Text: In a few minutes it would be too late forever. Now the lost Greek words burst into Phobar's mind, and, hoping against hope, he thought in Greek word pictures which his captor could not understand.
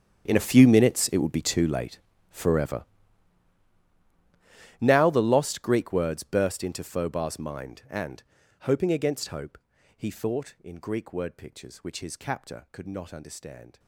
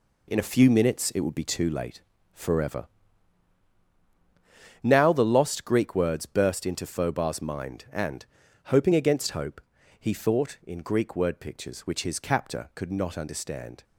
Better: second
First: gets quieter; strong; throughout; 19 dB // pauses between "late" and "forever"; slight; at 2.0 s; 0.32 s long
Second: pauses between "late" and "forever"; slight; at 2.0 s; 0.32 s long

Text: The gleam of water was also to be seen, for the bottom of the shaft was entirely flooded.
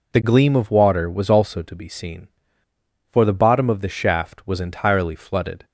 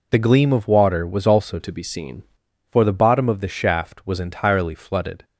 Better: first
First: none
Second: changes voice from "to" to "seen"; from 1.5 to 2.2 s; 0.7 s long

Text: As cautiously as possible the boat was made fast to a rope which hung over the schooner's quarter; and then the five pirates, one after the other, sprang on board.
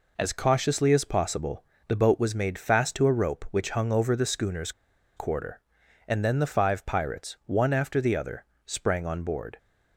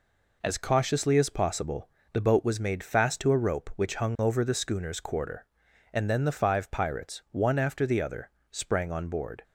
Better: second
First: pauses between "possible" and "the"; slight; at 1.6 s; 0.24 s long // pauses between "schooner's" and "quarter"; noticeable; at 4.7 s; 0.46 s long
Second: pauses between "possible" and "the"; slight; at 1.8 s; 0.24 s long

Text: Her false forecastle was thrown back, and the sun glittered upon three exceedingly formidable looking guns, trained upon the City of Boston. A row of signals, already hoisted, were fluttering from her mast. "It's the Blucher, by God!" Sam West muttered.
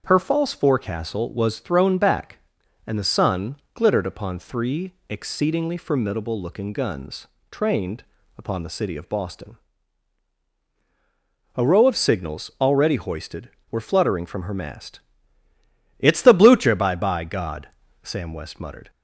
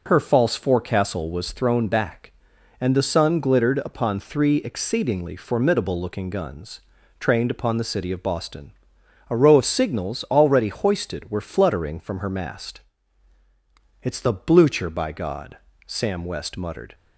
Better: second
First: starts louder than the rest; until 1.0 s; 7 dB // pauses between "sun" and "glittered"; slight; at 3.5 s; 0.18 s long // pauses between "three" and "exceedingly"; slight; at 4.9 s; 0.16 s long // pauses between "trained" and "upon"; slight; at 8.0 s; 0.34 s long // says "by" twice; at 16.9 s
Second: none

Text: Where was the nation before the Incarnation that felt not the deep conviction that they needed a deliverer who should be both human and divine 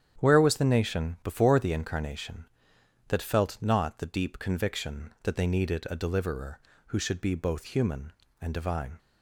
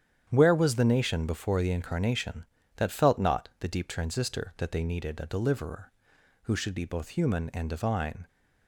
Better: first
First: starts louder than the rest; strong; until 1.2 s; 9 dB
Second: starts louder than the rest; strong; until 1.3 s; 9 dB // says "transistor" for "conviction"; at 3.8 s

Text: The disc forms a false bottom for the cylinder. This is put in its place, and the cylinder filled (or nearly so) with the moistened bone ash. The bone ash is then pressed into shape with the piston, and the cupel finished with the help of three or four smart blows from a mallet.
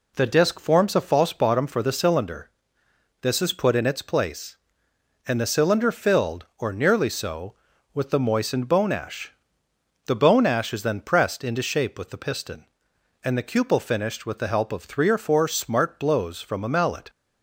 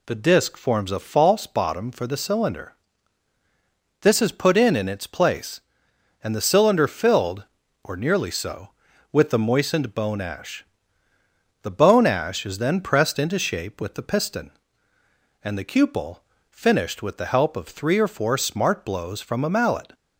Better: first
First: none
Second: says "in" twice; at 4.7 s // pauses between "cupel" and "finished"; slight; at 16.1 s; 0.30 s long

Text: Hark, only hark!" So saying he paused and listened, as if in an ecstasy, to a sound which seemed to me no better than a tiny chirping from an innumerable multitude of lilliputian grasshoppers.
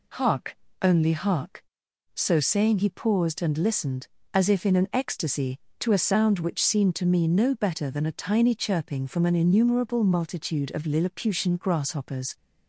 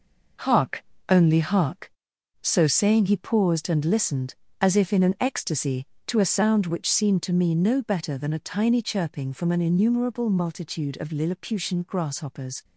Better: first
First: none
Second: gets quieter; throughout; 7 dB

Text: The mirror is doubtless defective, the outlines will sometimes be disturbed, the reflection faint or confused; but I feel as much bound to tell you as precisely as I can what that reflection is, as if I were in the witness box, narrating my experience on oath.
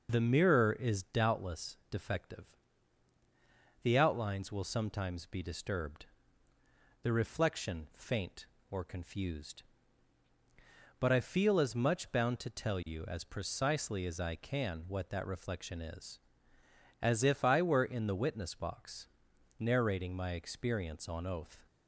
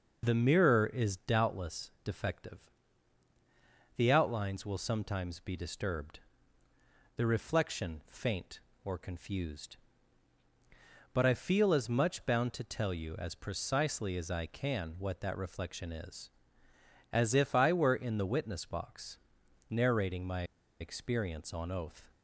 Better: first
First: none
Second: pauses between "my" and "experience"; at 20.4 s; 0.36 s long

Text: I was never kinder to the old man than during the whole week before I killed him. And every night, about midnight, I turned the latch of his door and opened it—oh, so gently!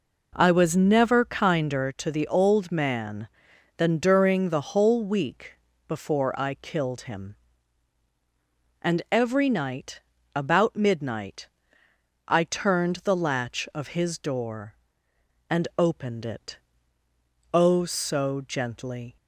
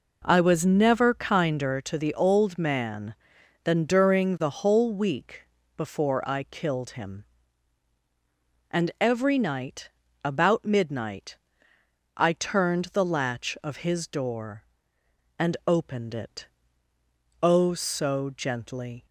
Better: neither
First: pauses between "week" and "before"; slight; at 5.5 s; 0.32 s long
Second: pauses between "week" and "before"; slight; at 5.4 s; 0.32 s long

